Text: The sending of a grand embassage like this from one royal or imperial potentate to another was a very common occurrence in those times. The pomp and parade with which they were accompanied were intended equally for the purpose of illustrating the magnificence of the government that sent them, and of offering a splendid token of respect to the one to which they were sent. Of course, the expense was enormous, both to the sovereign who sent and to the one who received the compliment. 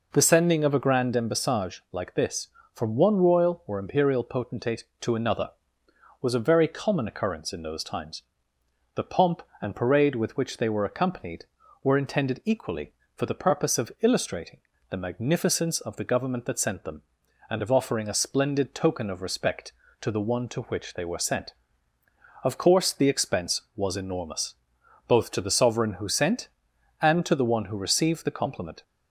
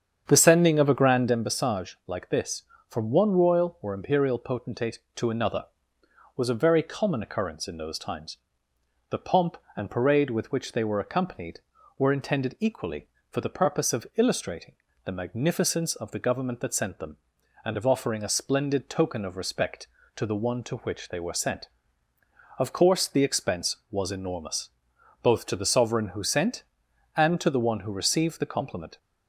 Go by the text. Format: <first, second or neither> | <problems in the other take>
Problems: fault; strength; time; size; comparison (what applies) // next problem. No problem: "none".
first | starts louder than the rest; strong; until 1.5 s; 8 dB // pauses between "illustrating" and "the"; slight; at 14.7 s; 0.30 s long; slight in the first